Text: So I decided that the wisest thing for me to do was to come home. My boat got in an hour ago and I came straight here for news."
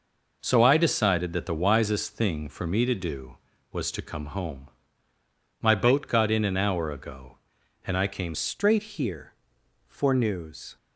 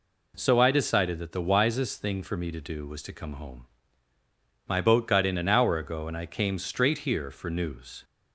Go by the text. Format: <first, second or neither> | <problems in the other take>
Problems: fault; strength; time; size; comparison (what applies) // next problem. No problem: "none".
second | changes voice at "straight"; from 8.3 s on; 2.4 s long